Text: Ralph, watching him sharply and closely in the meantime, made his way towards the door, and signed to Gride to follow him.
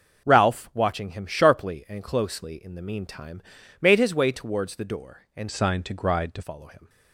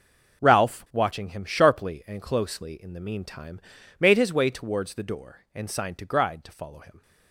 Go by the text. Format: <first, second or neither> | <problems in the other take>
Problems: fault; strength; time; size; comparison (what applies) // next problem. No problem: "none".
second | changes voice from "signed" to "to"; from 5.5 to 6.4 s; 0.9 s long